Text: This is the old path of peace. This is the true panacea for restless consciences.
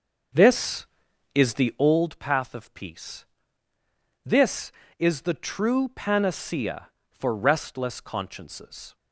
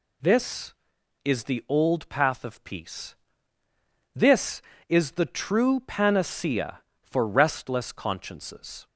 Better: second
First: starts louder than the rest; until 2.1 s; 6.5 dB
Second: none

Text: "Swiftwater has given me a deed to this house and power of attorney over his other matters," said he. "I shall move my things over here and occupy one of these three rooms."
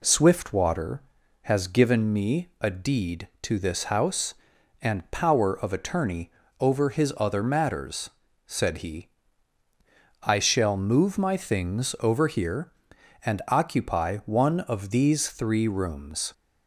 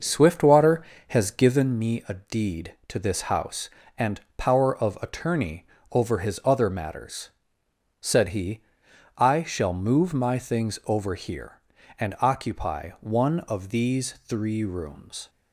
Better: first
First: pauses between "attorney" and "over"; slight; at 6.2 s; 0.30 s long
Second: starts louder than the rest; noticeable; until 1.7 s; 6 dB // pauses between "and" and "power"; slight; at 4.1 s; 0.16 s long // pauses between "attorney" and "over"; slight; at 5.6 s; 0.24 s long

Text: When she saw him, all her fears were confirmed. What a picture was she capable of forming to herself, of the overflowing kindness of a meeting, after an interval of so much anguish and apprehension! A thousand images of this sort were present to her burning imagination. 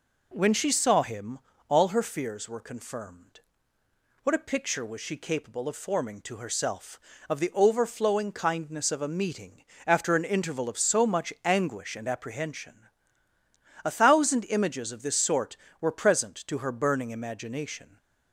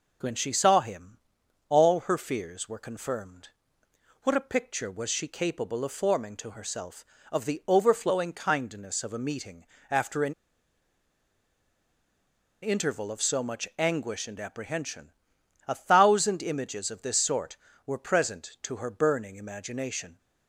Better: first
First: none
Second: pauses between "an" and "interval"; strong; at 10.3 s; 2.2 s long

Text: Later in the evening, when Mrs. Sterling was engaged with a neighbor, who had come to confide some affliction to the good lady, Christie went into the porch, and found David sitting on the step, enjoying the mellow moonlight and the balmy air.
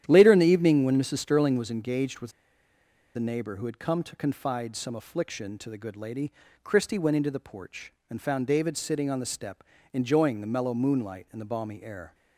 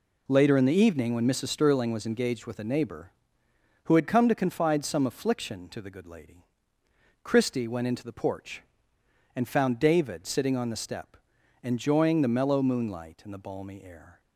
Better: second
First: starts louder than the rest; strong; until 1.0 s; 10.5 dB // pauses between "with" and "a"; noticeable; at 2.3 s; 0.84 s long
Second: none

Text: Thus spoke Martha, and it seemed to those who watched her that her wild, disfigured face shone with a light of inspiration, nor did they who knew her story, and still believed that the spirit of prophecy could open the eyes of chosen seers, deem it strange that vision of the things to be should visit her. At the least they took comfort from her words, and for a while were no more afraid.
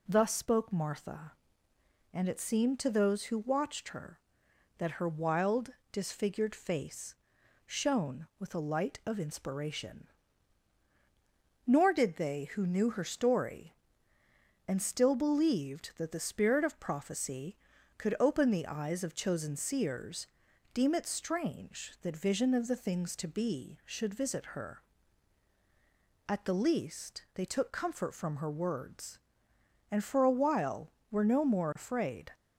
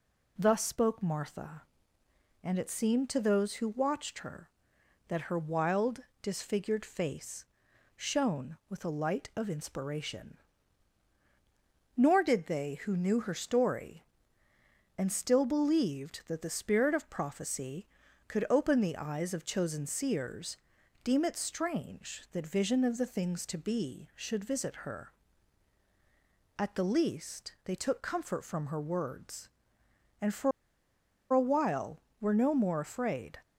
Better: first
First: pauses between "face" and "shone"; noticeable; at 7.1 s; 0.52 s long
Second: pauses between "face" and "shone"; noticeable; at 7.4 s; 0.52 s long // pauses between "for" and "a"; noticeable; at 30.5 s; 0.82 s long

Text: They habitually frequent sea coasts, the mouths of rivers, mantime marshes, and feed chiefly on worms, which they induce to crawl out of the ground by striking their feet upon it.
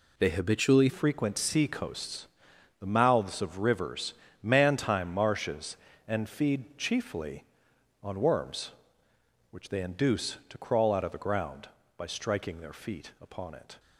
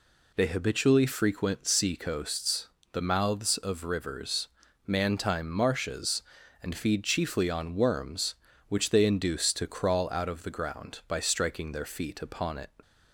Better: second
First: changes voice at "frequent"; from 0.8 s on; 12.9 s long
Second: none

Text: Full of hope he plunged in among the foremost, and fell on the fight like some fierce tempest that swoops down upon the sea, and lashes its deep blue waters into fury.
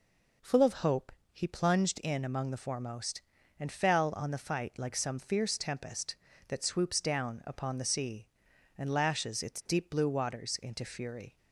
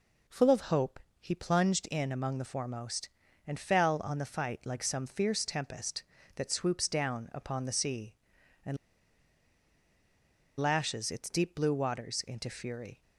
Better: first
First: pauses between "hope" and "he"; slight; at 1.1 s; 0.22 s long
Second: pauses between "hope" and "he"; slight; at 0.9 s; 0.22 s long // pauses between "and" and "lashes"; strong; at 8.7 s; 1.8 s long

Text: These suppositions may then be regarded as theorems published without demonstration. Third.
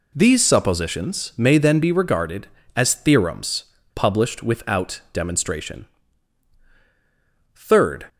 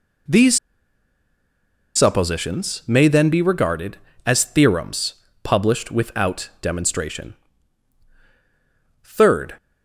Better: first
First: pauses between "theorems" and "published"; slight; at 3.6 s; 0.31 s long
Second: pauses between "These" and "suppositions"; strong; at 0.5 s; 1.3 s long // pauses between "theorems" and "published"; slight; at 5.1 s; 0.30 s long

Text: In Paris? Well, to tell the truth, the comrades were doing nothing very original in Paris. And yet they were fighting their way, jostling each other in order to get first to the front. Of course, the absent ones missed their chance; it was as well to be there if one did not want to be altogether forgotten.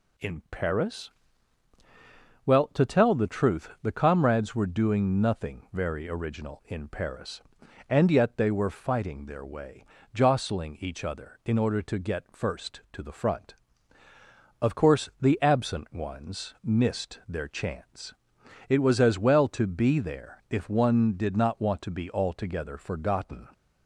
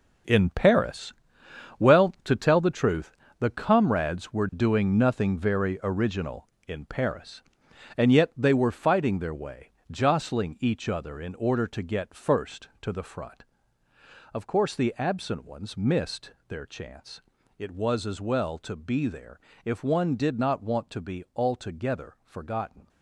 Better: first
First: none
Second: gets quieter; strong; throughout; 10 dB // pauses between "missed" and "their"; slight; at 16.3 s; 0.16 s long // pauses between "there" and "if"; slight; at 19.3 s; 0.26 s long

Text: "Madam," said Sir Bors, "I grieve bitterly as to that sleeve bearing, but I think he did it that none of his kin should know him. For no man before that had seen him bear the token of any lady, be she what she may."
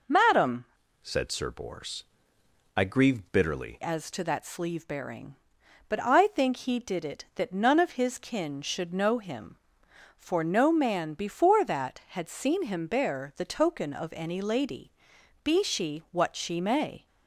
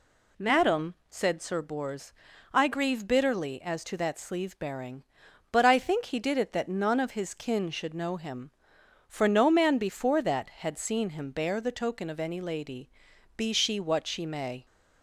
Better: second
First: changes voice from "said" to "bitterly"; from 1.0 to 3.8 s; 2.8 s long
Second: none

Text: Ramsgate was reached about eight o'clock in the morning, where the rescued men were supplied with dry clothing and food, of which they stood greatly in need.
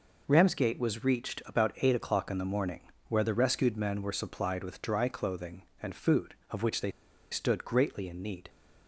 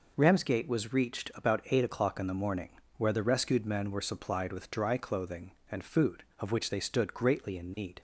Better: second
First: pauses between "they" and "stood"; at 6.8 s; 0.42 s long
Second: none

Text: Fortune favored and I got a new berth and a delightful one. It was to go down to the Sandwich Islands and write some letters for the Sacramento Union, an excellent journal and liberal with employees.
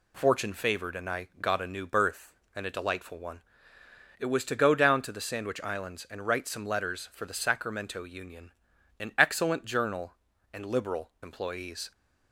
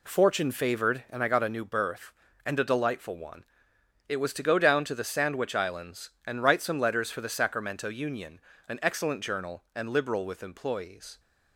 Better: second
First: skips "with"; at 11.1 s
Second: none

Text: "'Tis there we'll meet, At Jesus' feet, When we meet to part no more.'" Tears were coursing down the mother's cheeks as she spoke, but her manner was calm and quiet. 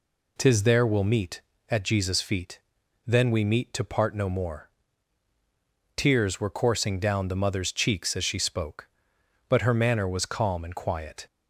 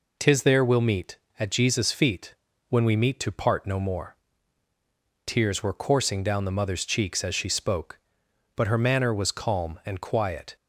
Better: second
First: says "Then" for "When"; at 3.0 s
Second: none

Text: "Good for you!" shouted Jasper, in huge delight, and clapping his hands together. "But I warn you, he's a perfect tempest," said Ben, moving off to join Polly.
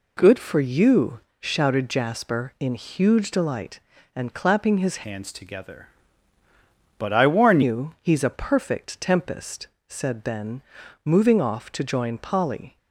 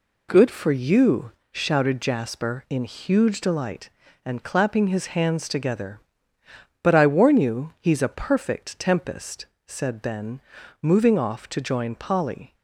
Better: second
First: changes voice from "hands" to "warn"; from 5.0 to 7.6 s; 2.6 s long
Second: none

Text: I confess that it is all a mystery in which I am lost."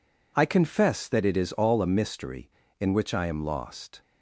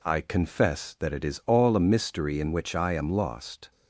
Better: neither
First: none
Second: none

